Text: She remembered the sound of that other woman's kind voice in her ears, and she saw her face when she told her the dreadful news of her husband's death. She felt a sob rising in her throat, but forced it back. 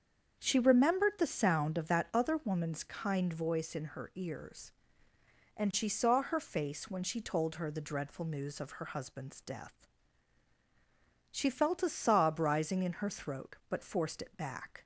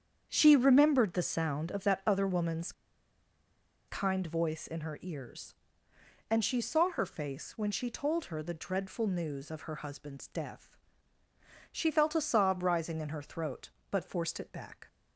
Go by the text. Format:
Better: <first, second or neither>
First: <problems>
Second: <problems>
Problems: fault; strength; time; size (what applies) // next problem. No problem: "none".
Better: first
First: starts louder than the rest; until 1.4 s; 7 dB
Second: starts louder than the rest; strong; until 1.3 s; 8 dB // pauses between "woman's" and "kind"; at 2.7 s; 1.1 s long